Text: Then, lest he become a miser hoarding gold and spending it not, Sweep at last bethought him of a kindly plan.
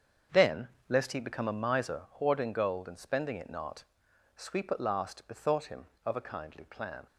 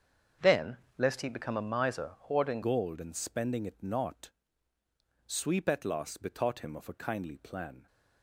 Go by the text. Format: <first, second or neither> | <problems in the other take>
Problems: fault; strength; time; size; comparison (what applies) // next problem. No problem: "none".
first | starts louder than the rest; strong; until 1.6 s; 7.5 dB; also in the first // changes voice at "gold"; from 2.6 s on; 5.2 s long